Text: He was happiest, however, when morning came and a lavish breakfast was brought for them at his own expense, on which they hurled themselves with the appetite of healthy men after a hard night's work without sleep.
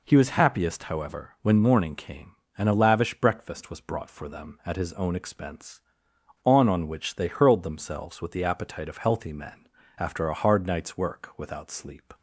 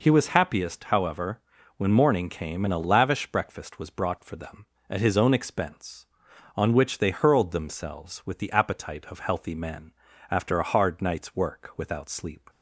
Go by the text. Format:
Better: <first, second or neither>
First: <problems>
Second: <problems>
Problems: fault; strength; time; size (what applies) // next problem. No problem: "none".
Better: second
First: says "on" twice; at 6.6 s // pauses between "men" and "after"; slight; at 9.6 s; 0.32 s long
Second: pauses between "men" and "after"; slight; at 9.9 s; 0.36 s long